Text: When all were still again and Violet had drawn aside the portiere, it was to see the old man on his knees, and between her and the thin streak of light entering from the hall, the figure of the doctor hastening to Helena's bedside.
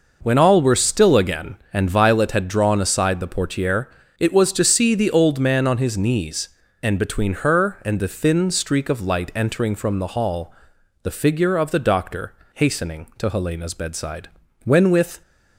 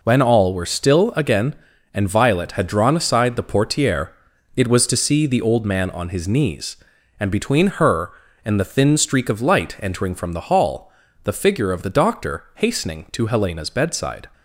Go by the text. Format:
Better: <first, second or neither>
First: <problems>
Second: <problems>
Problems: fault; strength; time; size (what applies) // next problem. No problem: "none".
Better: second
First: pauses between "doctor" and "hastening"; slight; at 12.3 s; 0.22 s long // goes on to say "When with"; from 14.6 s on; 0.58 s long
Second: none